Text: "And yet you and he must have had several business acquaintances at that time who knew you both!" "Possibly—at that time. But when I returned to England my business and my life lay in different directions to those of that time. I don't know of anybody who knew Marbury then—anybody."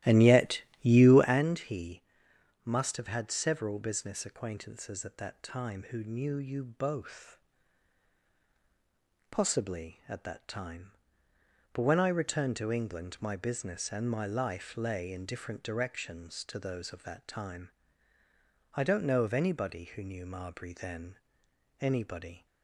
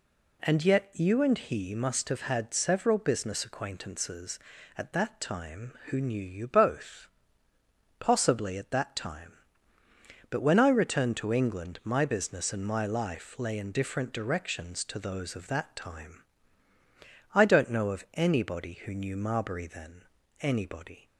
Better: second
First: starts louder than the rest; strong; until 1.4 s; 14.5 dB // pauses between "yet" and "you"; slight; at 0.6 s; 0.20 s long // pauses between "he" and "must"; noticeable; at 2.0 s; 0.60 s long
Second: none

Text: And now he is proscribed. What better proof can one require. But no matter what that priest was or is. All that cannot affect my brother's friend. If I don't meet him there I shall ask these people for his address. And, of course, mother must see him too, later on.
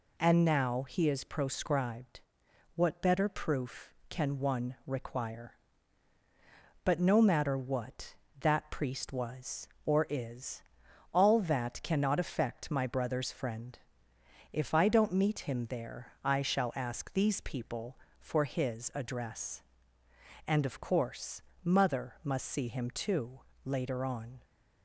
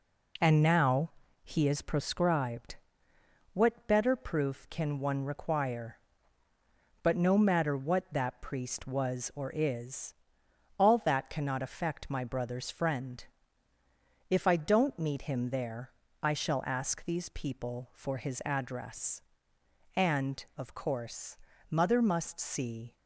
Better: first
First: none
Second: pauses between "now" and "he"; slight; at 1.1 s; 0.32 s long // pauses between "there" and "I"; slight; at 15.9 s; 0.32 s long // stops before "him too later on"; at 22.9 s

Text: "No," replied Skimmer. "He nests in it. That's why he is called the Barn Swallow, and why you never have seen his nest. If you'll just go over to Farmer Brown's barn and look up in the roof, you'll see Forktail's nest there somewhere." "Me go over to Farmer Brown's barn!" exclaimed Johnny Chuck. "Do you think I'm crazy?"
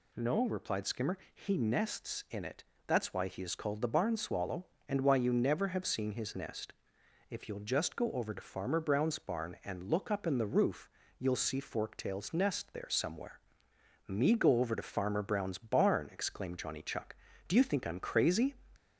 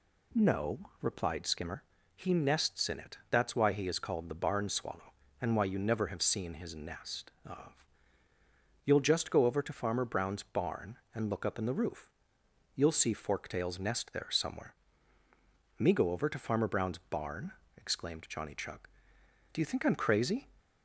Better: first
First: none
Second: says "Of" for "If"; at 7.4 s

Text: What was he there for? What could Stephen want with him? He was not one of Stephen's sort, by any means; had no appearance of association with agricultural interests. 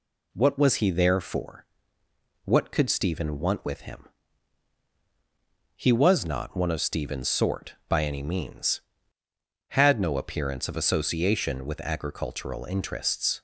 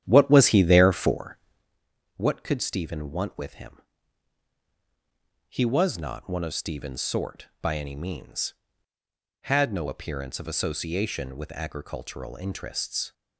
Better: first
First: none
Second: starts louder than the rest; strong; until 1.8 s; 10.5 dB

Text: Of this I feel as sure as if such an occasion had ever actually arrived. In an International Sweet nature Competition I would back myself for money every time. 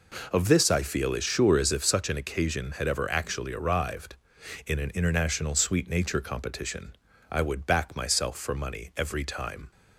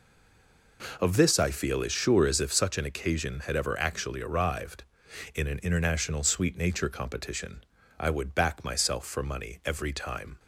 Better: first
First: pauses between "Competition" and "I"; slight; at 6.9 s; 0.36 s long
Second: stays silent before the first word; slight; until 0.7 s; 0.7 s long // pauses between "Competition" and "I"; slight; at 7.6 s; 0.36 s long

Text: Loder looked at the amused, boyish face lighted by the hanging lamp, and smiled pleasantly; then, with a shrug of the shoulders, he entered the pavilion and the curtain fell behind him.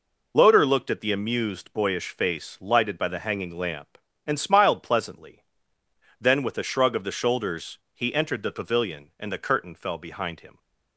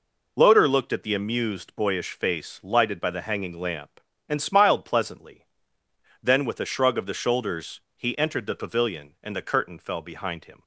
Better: neither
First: none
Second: none

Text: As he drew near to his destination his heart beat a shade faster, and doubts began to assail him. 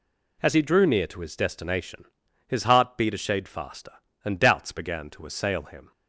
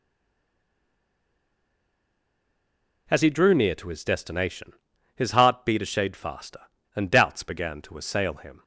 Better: first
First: pauses between "destination" and "his"; at 2.0 s; 0.44 s long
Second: stays silent before the first word; strong; until 3.0 s; 3.0 s long // pauses between "destination" and "his"; at 4.7 s; 0.44 s long

